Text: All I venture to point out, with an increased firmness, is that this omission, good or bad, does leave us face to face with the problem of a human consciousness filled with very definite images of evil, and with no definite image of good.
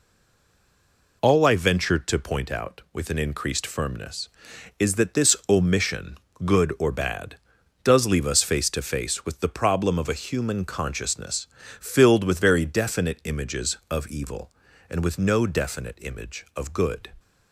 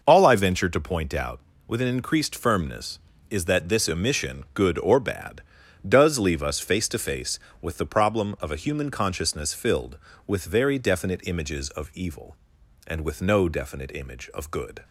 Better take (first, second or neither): second